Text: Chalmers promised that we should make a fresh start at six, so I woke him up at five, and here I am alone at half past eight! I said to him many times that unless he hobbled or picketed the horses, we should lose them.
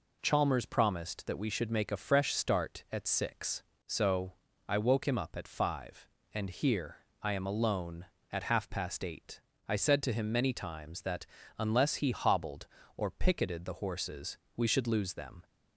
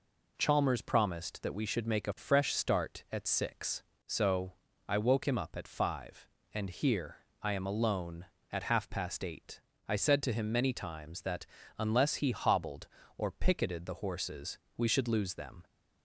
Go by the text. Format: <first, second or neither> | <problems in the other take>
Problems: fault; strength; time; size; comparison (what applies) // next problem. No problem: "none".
neither | pauses between "so" and "I"; slight; the same in both // pauses between "here" and "I"; slight; the same in both // pauses between "that" and "unless"; slight; the same in both